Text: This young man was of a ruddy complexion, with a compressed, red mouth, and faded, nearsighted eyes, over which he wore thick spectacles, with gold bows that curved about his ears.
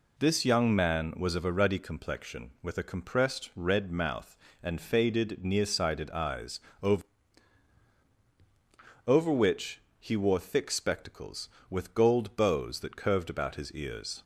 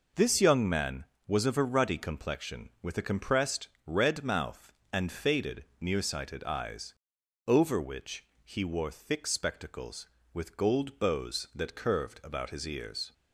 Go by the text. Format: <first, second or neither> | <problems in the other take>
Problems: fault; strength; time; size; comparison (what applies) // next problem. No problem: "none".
second | says "over" twice; at 9.0 s // pauses between "which" and "he"; slight; at 9.7 s; 0.22 s long; slight in the second